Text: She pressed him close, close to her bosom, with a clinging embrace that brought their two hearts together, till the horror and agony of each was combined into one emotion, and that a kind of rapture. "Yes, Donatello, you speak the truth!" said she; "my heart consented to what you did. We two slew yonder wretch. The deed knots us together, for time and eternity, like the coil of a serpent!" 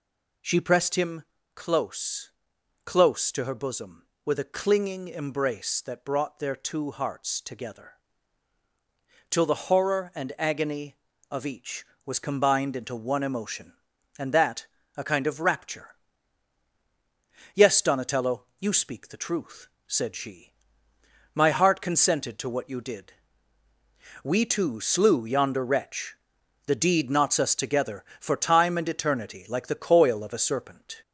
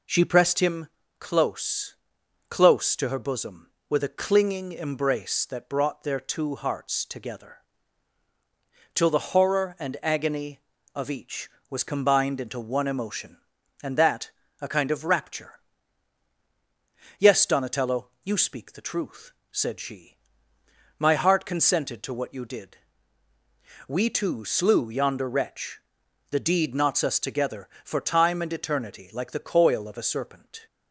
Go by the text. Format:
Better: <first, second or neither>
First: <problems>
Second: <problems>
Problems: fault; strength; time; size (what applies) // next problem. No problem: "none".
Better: second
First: gets louder; slight; throughout; 3 dB // pauses between "him" and "close"; slight; at 1.2 s; 0.32 s long // pauses between "that" and "a"; slight; at 14.6 s; 0.30 s long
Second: pauses between "him" and "close"; slight; at 0.8 s; 0.32 s long // pauses between "that" and "a"; slight; at 14.2 s; 0.30 s long